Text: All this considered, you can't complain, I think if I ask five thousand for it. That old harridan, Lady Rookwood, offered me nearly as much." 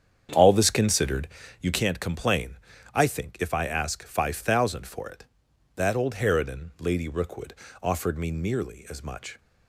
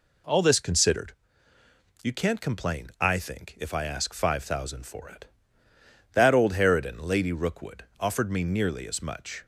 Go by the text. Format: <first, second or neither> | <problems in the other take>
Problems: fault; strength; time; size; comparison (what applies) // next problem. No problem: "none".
second | starts louder than the rest; strong; until 1.4 s; 8 dB